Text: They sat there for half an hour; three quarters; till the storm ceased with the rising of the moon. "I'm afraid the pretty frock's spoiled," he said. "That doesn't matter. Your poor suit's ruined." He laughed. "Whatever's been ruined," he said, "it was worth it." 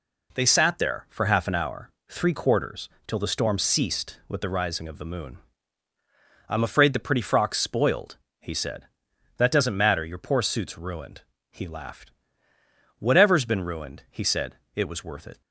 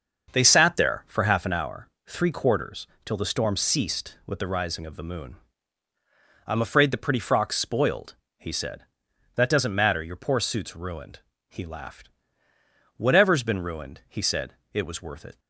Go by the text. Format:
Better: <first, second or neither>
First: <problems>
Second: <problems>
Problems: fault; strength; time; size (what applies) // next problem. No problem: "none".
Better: first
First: none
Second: starts louder than the rest; until 1.3 s; 6.5 dB